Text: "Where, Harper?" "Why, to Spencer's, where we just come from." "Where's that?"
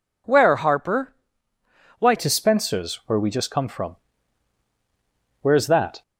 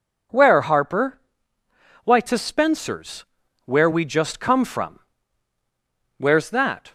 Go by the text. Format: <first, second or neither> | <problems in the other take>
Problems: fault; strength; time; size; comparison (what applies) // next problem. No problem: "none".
second | changes voice at "to"; from 2.1 s on; 3.9 s long